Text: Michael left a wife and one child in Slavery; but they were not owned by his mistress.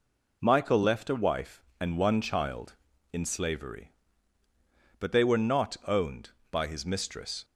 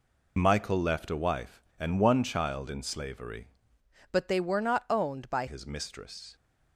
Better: first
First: none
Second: changes voice from "but" to "by"; from 4.1 to 5.4 s; 1.3 s long

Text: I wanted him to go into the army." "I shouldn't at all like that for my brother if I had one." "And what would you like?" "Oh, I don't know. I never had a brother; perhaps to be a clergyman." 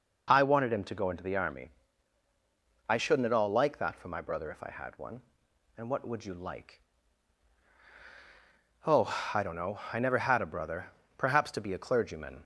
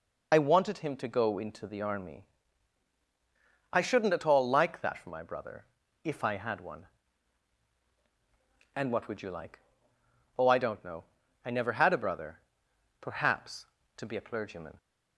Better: first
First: none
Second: loses the start of "I"; at 0.3 s; 45 ms // pauses between "brother" and "if"; at 5.6 s; 0.38 s long

